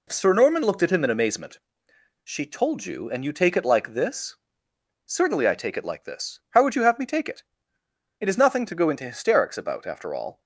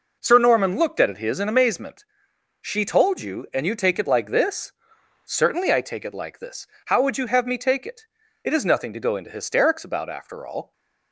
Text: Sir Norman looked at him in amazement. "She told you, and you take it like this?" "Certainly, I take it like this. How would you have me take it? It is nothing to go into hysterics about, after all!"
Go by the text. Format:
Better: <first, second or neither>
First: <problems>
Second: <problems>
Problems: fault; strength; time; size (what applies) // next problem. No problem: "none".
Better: first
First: none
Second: says "his" for "him"; at 1.1 s